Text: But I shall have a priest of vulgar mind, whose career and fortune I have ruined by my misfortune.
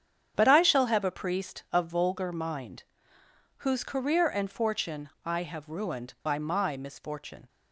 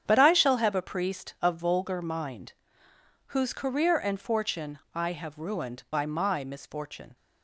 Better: neither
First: starts louder than the rest; strong; until 1.3 s; 8.5 dB // pauses between "fortune" and "I"; slight; at 5.0 s; 0.16 s long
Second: starts louder than the rest; strong; until 1.0 s; 8.5 dB // pauses between "fortune" and "I"; slight; at 4.7 s; 0.16 s long

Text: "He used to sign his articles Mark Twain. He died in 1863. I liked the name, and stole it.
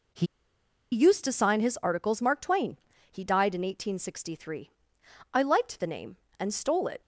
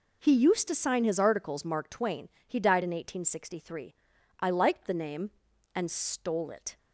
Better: second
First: pauses between "He" and "used"; noticeable; at 0.2 s; 0.66 s long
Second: none

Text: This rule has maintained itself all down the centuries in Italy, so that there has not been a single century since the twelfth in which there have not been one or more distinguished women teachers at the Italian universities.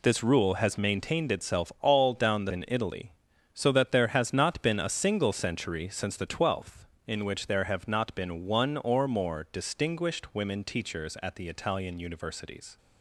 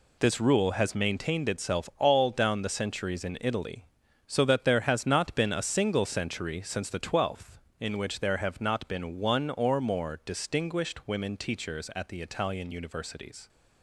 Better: second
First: skips "centuries"; at 2.5 s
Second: none

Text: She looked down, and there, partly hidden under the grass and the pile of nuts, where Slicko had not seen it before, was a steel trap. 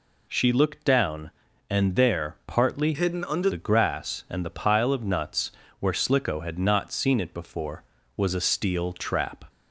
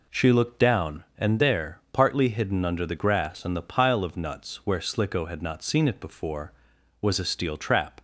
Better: second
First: changes voice from "hidden" to "under"; from 2.9 to 3.4 s; 0.5 s long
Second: none

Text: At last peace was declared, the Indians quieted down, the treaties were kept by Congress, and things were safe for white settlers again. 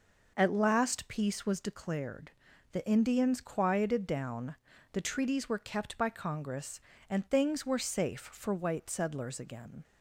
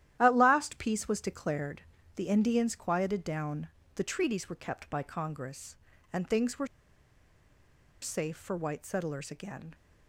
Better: first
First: none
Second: starts louder than the rest; strong; until 1.2 s; 12 dB // pauses between "were" and "safe"; strong; at 6.6 s; 1.3 s long

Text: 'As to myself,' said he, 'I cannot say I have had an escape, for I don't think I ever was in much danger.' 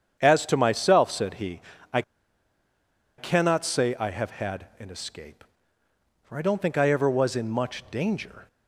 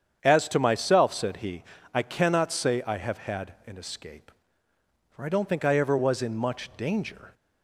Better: second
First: starts louder than the rest; strong; until 1.2 s; 8 dB // pauses between "I" and "cannot"; at 2.0 s; 1.1 s long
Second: starts louder than the rest; strong; until 1.2 s; 8 dB

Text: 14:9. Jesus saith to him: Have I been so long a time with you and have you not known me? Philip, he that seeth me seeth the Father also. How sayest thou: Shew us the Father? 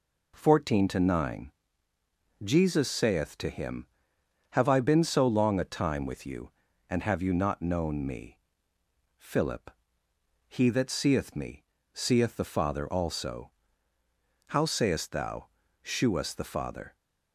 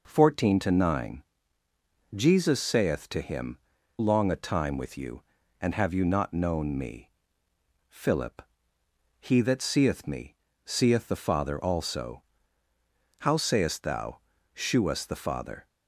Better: first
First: pauses between "me" and "seeth"; slight; at 11.6 s; 0.30 s long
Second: skips "Have I been so"; at 3.7 s // pauses between "me" and "seeth"; slight; at 10.3 s; 0.30 s long

